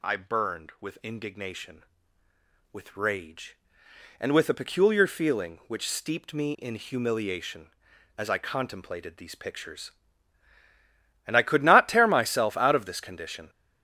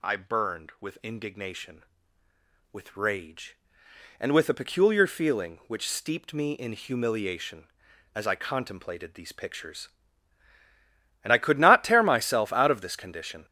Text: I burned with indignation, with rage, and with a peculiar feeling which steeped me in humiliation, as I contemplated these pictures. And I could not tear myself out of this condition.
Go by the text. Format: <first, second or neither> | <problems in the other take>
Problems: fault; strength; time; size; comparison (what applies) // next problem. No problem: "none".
neither | none